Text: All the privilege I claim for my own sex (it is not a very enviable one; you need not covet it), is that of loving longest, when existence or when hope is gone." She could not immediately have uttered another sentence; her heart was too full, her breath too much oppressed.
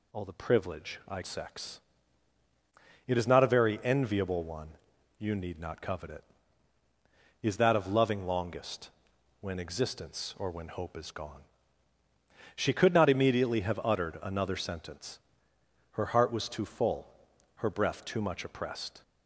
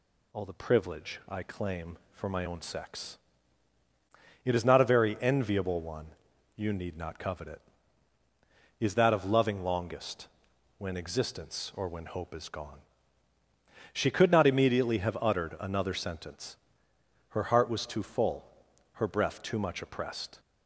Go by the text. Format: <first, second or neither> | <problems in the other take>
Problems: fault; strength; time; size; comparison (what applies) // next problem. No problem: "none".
second | skips "claim for my own"; at 1.2 s